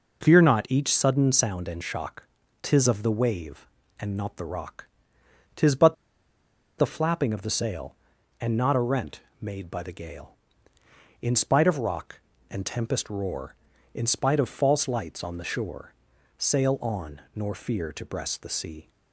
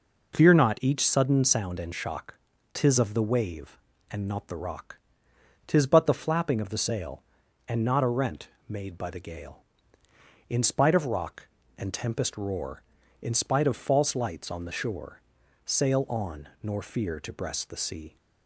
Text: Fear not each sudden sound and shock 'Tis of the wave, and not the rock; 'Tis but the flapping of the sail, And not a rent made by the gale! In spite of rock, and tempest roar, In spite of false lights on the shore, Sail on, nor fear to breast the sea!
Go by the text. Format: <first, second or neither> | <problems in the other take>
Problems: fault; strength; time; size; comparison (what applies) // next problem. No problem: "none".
second | pauses between "shock" and "Tis"; slight; at 2.2 s; 0.34 s long; slight in the second // pauses between "but" and "the"; noticeable; at 5.9 s; 0.83 s long // pauses between "rent" and "made"; slight; at 9.2 s; 0.18 s long; slight in the second